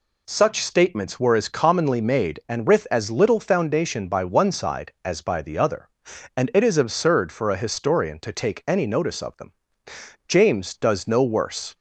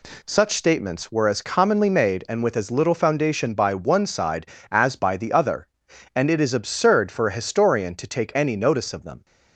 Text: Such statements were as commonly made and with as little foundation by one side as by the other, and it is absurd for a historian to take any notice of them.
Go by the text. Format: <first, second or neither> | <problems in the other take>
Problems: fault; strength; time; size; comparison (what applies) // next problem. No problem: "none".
second | goes on to say "James does no worse"; from 10.2 s on; 1.4 s long